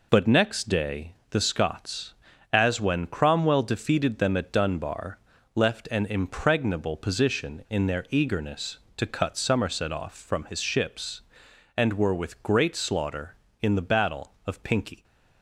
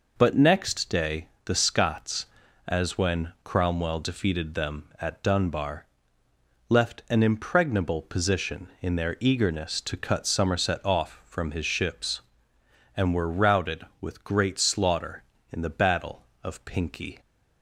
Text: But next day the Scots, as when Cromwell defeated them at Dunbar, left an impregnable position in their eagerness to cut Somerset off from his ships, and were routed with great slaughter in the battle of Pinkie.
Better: second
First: pauses between "day" and "the"; slight; at 1.1 s; 0.16 s long // skips "routed"; at 12.1 s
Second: pauses between "day" and "the"; slight; at 1.2 s; 0.18 s long

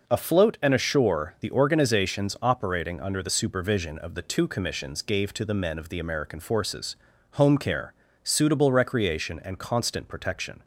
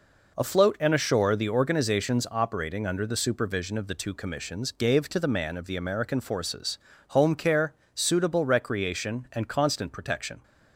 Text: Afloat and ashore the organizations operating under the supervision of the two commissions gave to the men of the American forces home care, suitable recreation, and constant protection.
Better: first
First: pauses between "forces" and "home"; at 6.9 s; 0.36 s long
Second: says "man" for "men"; at 5.2 s // pauses between "forces" and "home"; slight; at 6.7 s; 0.30 s long

